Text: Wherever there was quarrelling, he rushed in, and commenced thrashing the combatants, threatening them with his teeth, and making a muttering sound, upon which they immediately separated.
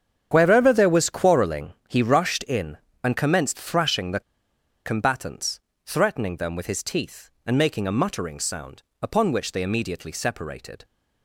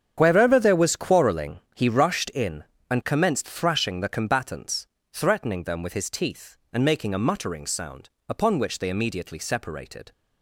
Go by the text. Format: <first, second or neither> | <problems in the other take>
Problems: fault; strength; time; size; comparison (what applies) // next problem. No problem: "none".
second | starts louder than the rest; strong; until 1.3 s; 8 dB; strong in the second // pauses between "the" and "combatants"; noticeable; at 4.2 s; 0.64 s long